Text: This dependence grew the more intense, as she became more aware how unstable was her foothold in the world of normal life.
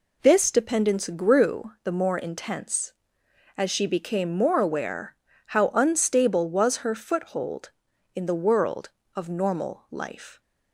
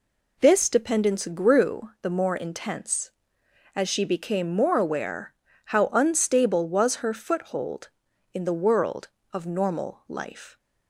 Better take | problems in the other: neither | pauses between "aware" and "how"; slight; the same in both

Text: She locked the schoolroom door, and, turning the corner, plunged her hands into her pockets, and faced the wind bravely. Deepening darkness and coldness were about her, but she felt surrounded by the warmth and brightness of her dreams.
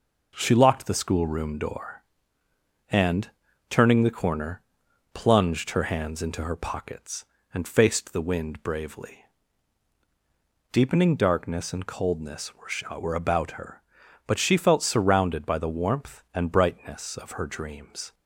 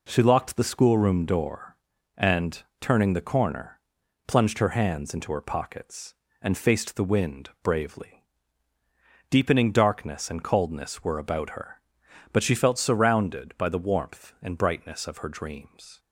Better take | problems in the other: second | says "were" twice; at 12.9 s

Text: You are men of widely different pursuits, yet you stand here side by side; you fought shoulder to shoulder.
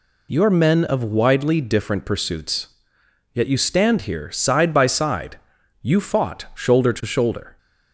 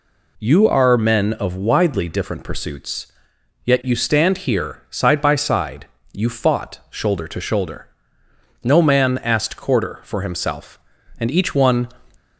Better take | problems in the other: first | goes on to say "No man asked quarter for himself and each one"; strong; from 8.6 s on; 3.2 s long

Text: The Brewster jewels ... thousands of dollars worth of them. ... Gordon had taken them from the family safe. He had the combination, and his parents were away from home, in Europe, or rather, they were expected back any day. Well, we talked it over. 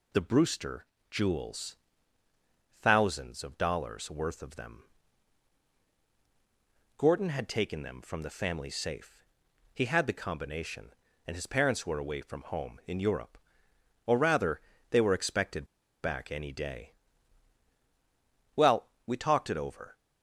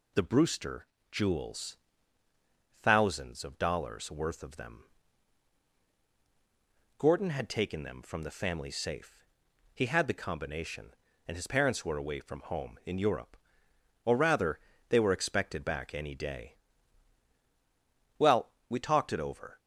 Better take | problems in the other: second | pauses between "Brewster" and "jewels"; slight; at 0.8 s; 0.24 s long; slight in the second // pauses between "expected" and "back"; at 15.6 s; 0.36 s long

